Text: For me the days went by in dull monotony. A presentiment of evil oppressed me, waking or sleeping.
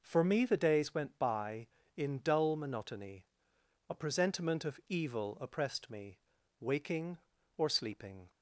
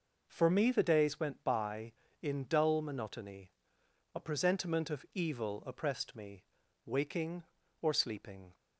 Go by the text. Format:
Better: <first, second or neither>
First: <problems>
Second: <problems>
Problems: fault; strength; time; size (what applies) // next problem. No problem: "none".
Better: neither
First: none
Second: none